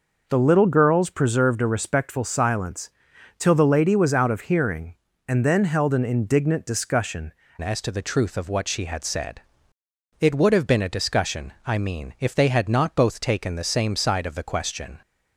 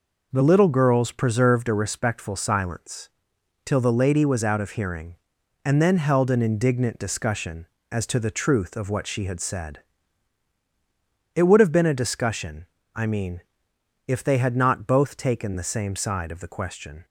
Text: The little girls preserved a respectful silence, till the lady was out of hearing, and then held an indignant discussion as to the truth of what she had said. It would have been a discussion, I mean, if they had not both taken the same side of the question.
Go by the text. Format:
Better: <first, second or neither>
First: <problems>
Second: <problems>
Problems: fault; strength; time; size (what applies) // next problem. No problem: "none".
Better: second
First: changes voice at "as"; from 7.6 s on; 7.4 s long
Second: none